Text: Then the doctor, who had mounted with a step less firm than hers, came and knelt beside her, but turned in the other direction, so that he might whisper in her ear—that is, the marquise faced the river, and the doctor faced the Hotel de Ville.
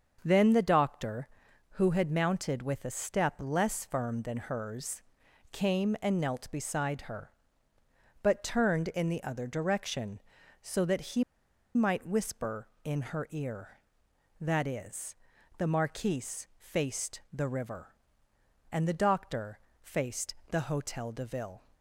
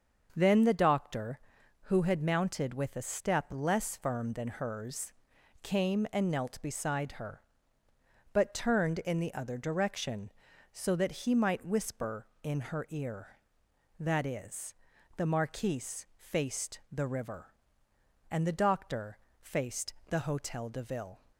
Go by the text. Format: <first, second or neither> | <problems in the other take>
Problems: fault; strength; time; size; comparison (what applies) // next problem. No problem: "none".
second | starts louder than the rest; until 1.2 s; 6.5 dB; also in the second // pauses between "he" and "might"; noticeable; at 11.2 s; 0.51 s long // pauses between "doctor" and "faced"; slight; at 19.5 s; 0.22 s long; slight in the second // pauses between "faced" and "the"; slight; at 20.3 s; 0.16 s long; slight in the second